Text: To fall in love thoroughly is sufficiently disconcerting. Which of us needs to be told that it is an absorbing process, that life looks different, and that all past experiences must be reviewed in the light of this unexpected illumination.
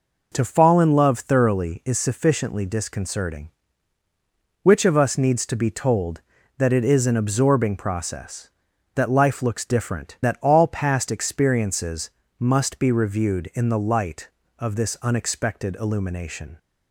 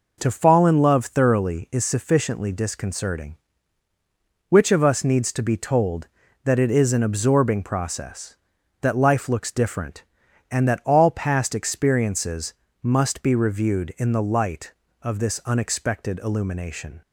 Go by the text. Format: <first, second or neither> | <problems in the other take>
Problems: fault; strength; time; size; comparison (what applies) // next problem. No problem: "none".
second | skips "and"; at 10.2 s // pauses between "experiences" and "must"; slight; at 12.0 s; 0.28 s long; slight in the second